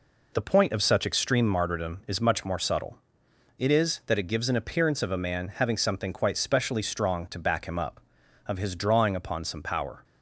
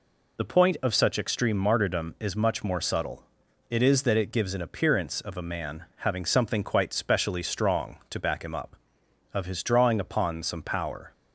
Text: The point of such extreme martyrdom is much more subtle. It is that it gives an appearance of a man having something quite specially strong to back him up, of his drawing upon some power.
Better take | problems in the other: neither | none

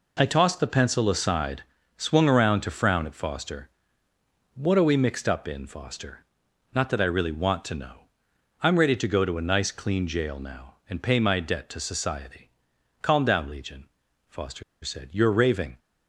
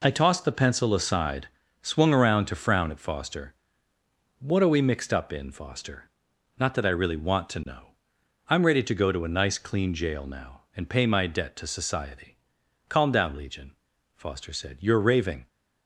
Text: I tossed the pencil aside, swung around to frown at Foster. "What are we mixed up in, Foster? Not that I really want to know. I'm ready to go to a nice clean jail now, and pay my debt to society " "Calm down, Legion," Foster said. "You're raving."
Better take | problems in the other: second | pauses between "Foster" and "said"; slight; at 14.6 s; 0.21 s long

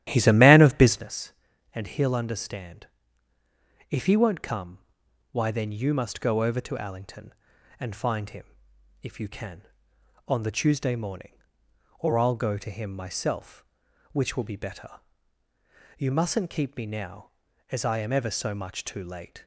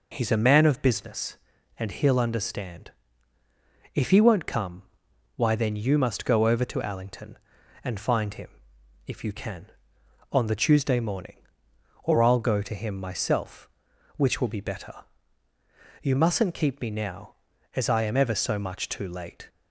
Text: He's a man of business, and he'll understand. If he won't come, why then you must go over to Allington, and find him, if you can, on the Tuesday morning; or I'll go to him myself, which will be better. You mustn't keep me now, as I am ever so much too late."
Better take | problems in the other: second | starts louder than the rest; strong; until 1.2 s; 12.5 dB

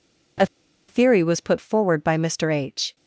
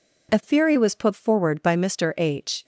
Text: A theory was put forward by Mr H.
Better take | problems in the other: second | pauses between "A" and "theory"; at 0.4 s; 0.43 s long

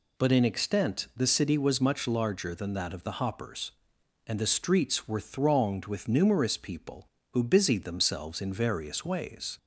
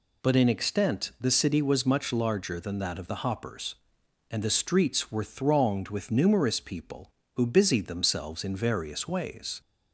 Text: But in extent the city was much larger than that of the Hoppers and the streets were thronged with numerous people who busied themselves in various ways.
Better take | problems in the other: neither | none

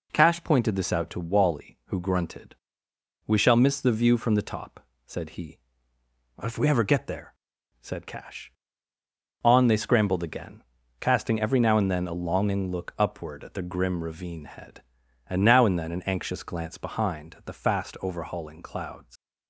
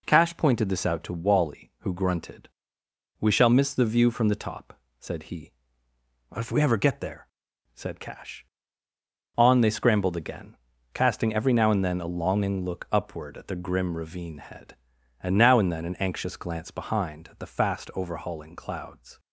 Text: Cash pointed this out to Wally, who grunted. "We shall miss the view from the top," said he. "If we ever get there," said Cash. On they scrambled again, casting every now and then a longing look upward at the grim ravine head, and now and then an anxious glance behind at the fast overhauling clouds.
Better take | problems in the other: second | leaves "clouds" unfinished; at 19.1 s; 100 ms

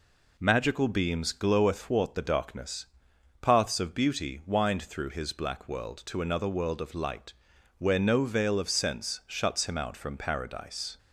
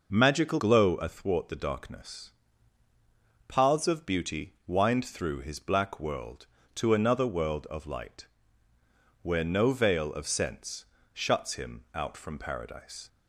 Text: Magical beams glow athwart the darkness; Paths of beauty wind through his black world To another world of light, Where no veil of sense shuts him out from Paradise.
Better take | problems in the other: first | skips "beams"; at 0.5 s // pauses between "sense" and "shuts"; slight; at 10.8 s; 0.30 s long

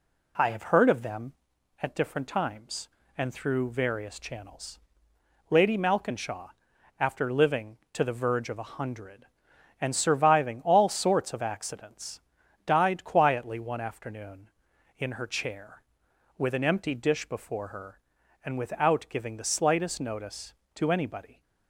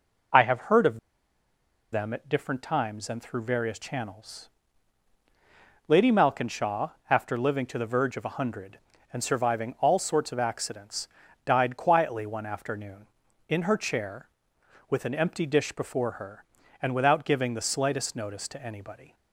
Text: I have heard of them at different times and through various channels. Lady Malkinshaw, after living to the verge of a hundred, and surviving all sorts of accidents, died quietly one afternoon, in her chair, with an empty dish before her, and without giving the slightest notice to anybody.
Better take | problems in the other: first | pauses between "of" and "them"; noticeable; at 0.9 s; 0.93 s long

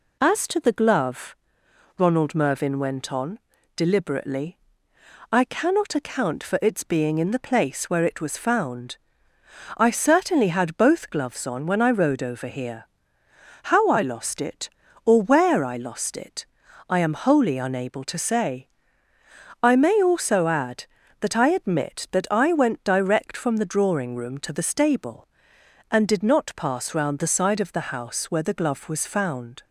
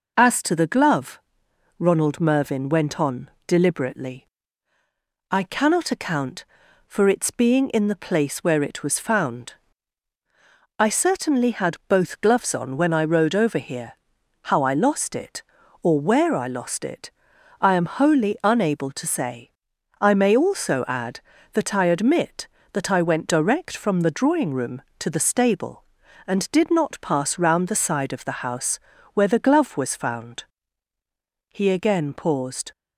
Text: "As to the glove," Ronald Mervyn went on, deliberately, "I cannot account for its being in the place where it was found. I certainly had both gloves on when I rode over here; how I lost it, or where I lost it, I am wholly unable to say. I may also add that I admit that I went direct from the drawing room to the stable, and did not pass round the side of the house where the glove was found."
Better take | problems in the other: first | pauses between "house" and "where"; slight; at 28.7 s; 0.36 s long // goes on to say "He again paused"; noticeable; from 31.4 s on; 1.2 s long

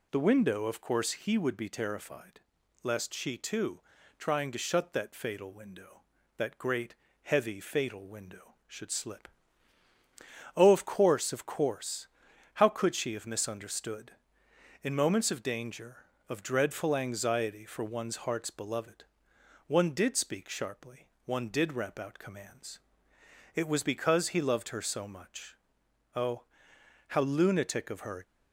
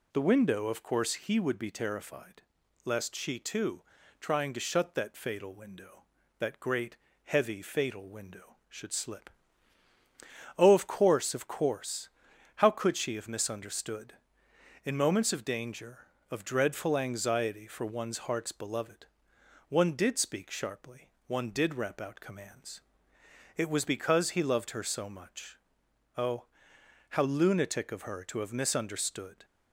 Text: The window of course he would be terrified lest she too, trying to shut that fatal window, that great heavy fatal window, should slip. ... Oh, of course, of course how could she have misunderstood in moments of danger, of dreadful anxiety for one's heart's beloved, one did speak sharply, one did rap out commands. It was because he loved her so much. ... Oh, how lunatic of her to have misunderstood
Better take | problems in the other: second | pauses between "terrified" and "lest"; at 2.4 s; 0.42 s long; also in the second // pauses between "great" and "heavy"; slight; at 6.9 s; 0.28 s long; slight in the second // pauses between "course" and "how"; noticeable; at 12.0 s; 0.48 s long; noticeable in the second // stops before "to have misunderstood"; at 28.2 s

